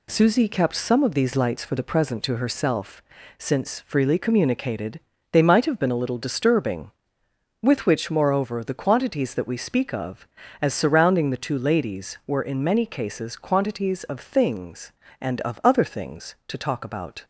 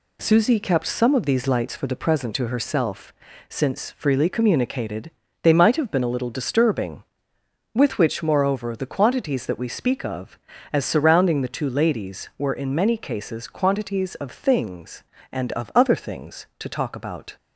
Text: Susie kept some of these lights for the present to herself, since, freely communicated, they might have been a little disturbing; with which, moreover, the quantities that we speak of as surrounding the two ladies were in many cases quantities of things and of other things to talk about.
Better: neither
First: none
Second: none

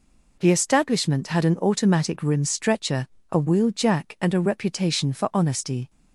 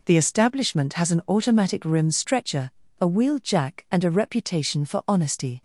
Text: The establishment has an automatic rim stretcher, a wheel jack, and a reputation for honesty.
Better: second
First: says "had" for "has"; at 1.2 s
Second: none

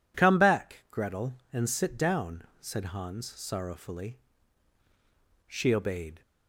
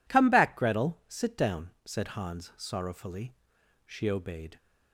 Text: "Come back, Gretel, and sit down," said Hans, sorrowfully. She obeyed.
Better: first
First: none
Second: skips "and"; at 1.0 s

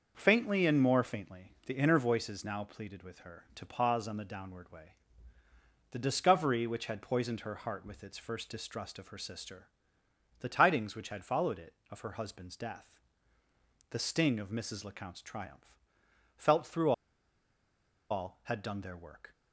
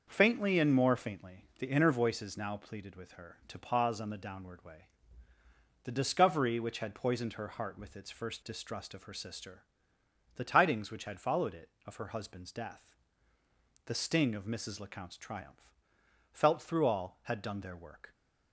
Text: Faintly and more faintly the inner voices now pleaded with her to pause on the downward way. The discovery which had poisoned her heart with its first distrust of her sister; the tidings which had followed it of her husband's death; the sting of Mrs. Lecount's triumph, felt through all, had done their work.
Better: second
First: starts louder than the rest; until 1.1 s; 6 dB // pauses between "through" and "all"; at 16.9 s; 1.1 s long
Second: starts louder than the rest; until 1.0 s; 6 dB

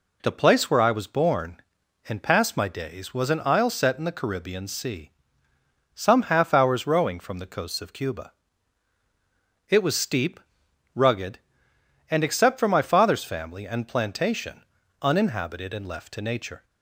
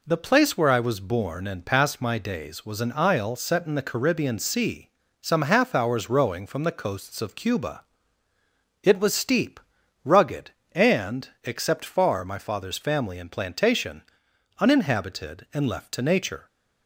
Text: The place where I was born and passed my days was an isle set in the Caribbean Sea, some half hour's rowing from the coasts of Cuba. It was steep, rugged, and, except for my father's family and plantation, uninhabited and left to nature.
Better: first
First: none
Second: says "far" for "for"; at 11.8 s

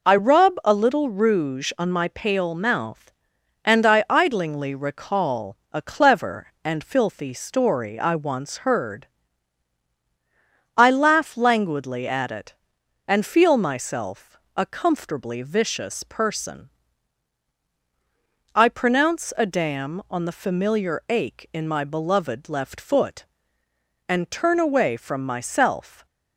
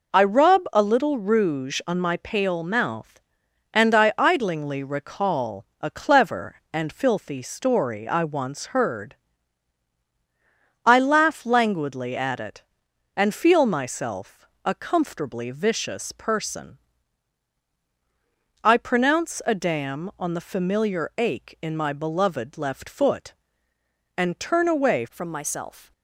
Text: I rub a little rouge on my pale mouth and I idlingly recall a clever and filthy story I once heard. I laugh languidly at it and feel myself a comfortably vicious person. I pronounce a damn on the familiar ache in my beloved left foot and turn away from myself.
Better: first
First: pauses between "myself" and "a"; slight; at 14.3 s; 0.18 s long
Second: pauses between "myself" and "a"; slight; at 14.4 s; 0.18 s long // changes voice at "from"; from 25.0 s on; 0.9 s long

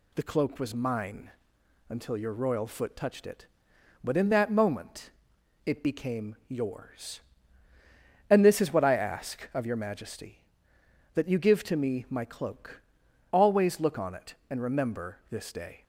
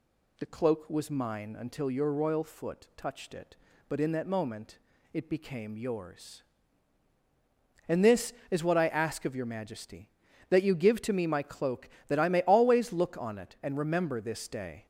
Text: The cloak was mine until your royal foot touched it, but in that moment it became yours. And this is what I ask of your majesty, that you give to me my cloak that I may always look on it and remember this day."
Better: second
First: pauses between "mine" and "until"; noticeable; at 1.3 s; 0.58 s long // pauses between "moment" and "it"; noticeable; at 5.1 s; 0.54 s long // skips "that I may"; at 13.0 s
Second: pauses between "moment" and "it"; slight; at 4.7 s; 0.34 s long

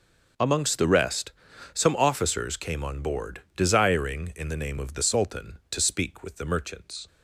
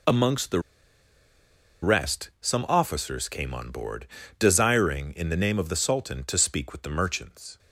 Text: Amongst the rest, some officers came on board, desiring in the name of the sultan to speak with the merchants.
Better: first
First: none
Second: pauses between "the" and "rest"; at 0.5 s; 1.2 s long

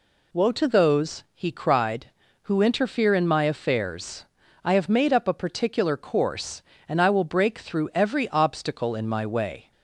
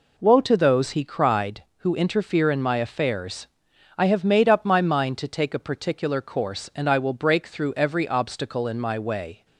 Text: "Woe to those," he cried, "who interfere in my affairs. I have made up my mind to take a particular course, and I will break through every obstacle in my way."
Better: second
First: skips "my mind to take"; at 5.2 s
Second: none

